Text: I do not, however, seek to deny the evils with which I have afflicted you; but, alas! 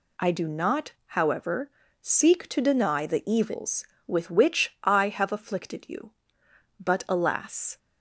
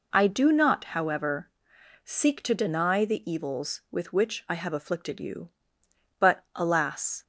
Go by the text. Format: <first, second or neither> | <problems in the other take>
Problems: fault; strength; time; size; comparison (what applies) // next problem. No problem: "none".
neither | none